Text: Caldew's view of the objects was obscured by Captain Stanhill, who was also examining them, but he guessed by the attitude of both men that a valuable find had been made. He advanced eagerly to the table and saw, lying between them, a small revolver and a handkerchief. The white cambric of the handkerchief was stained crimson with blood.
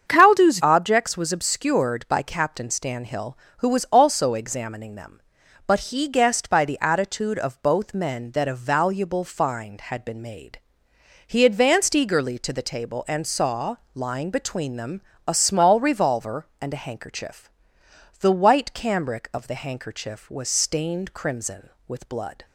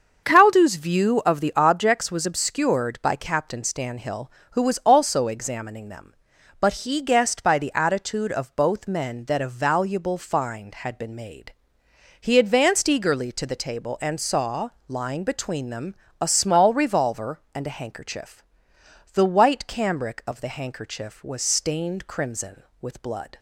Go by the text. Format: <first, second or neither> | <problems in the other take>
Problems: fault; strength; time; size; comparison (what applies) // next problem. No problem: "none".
second | starts louder than the rest; strong; until 1.1 s; 7 dB; also in the second // skips "view of the"; at 0.5 s